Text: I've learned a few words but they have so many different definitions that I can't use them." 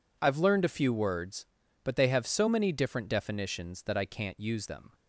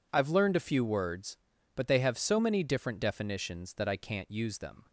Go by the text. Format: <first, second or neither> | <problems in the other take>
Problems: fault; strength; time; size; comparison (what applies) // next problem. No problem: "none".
neither | none